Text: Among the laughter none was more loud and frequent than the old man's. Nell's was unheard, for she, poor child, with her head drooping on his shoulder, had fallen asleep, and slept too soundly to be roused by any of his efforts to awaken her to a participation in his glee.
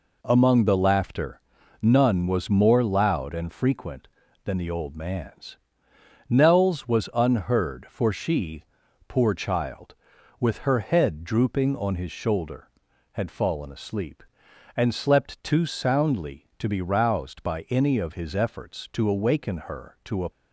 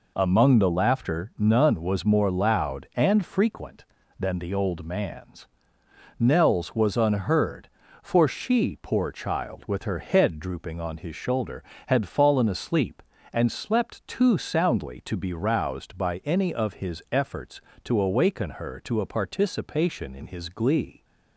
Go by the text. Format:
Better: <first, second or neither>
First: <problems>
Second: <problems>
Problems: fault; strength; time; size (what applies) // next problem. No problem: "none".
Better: second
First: pauses between "laughter" and "none"; at 1.3 s; 0.42 s long // stops before "participation in his glee"; at 20.3 s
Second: none